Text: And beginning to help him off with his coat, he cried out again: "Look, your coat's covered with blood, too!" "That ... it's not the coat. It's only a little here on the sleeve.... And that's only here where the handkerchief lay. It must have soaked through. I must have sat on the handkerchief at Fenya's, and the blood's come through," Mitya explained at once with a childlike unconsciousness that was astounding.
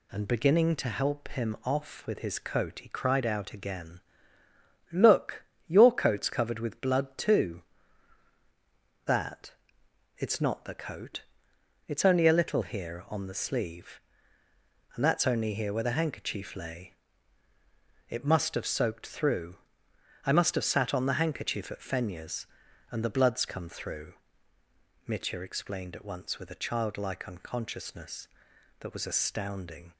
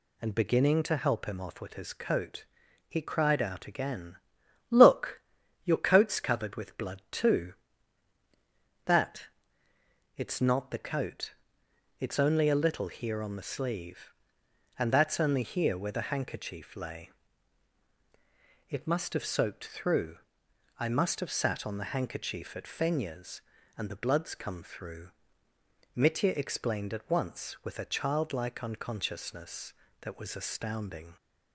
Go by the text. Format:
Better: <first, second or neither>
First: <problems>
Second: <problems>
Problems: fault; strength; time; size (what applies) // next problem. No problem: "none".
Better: neither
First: none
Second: none